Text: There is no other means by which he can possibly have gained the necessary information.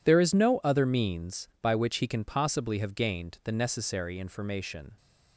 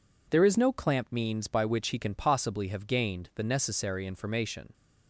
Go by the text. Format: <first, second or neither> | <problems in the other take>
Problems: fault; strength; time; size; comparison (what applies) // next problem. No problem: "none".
first | says "clamp" for "other"; at 0.7 s